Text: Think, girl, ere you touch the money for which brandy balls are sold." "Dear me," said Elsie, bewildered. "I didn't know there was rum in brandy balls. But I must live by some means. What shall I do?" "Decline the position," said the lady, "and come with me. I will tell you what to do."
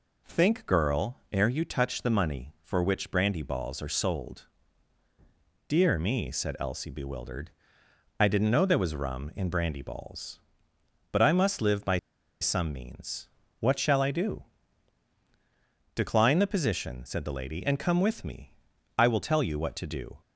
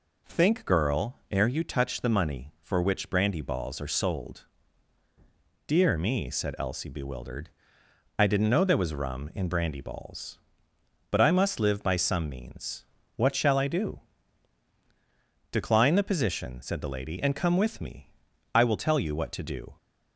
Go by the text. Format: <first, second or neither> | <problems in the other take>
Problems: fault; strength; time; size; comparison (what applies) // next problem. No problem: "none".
second | pauses between "by" and "some"; at 11.9 s; 0.43 s long